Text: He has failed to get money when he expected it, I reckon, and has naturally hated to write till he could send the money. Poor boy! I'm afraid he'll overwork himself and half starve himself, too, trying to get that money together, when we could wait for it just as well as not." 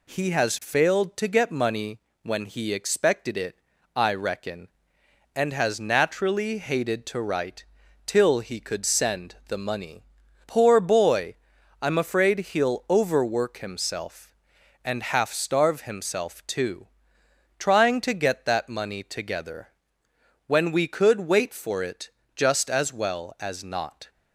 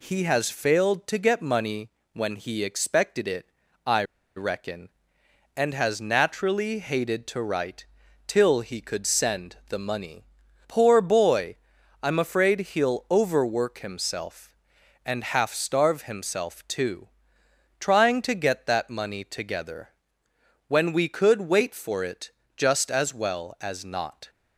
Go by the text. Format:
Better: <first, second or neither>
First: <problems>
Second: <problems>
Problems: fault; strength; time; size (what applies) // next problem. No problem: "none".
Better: first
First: pauses between "money" and "when"; slight; at 2.0 s; 0.22 s long // pauses between "write" and "till"; at 7.6 s; 0.42 s long // pauses between "it" and "just"; slight; at 22.0 s; 0.26 s long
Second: pauses between "money" and "when"; slight; at 1.9 s; 0.22 s long // pauses between "I" and "reckon"; slight; at 4.0 s; 0.32 s long // pauses between "write" and "till"; at 7.8 s; 0.42 s long // pauses between "it" and "just"; slight; at 22.2 s; 0.26 s long